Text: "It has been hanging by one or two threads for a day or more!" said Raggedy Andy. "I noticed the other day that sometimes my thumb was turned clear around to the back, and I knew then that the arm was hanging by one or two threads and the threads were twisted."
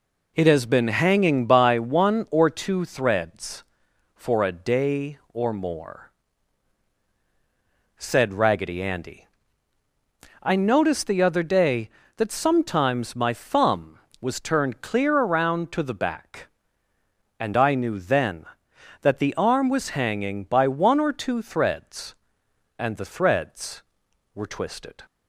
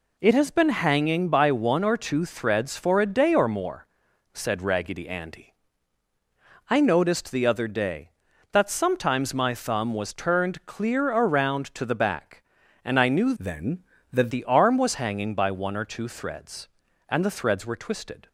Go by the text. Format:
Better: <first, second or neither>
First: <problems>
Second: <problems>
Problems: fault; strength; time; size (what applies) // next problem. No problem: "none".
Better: first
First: none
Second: changes voice from "then" to "that"; from 13.3 to 14.3 s; 1.0 s long